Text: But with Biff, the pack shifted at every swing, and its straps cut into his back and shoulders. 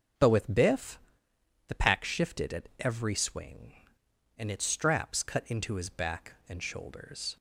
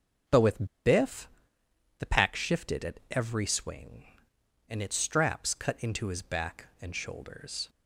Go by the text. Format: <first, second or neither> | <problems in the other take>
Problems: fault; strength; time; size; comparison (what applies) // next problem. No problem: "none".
first | starts louder than the rest; until 2.2 s; 6.5 dB; also in the first // pauses between "with" and "Biff"; slight; at 0.6 s; 0.20 s long